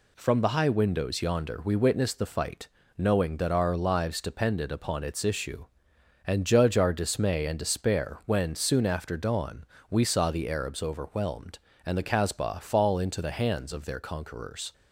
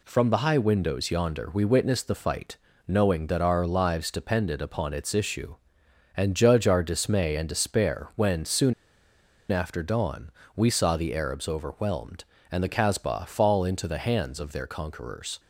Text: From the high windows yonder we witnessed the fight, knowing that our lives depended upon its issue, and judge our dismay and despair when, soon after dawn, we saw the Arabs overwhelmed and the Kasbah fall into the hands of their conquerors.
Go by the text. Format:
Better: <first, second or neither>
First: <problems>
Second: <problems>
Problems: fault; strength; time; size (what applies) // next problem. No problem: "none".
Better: first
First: none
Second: pauses between "soon" and "after"; noticeable; at 8.7 s; 0.78 s long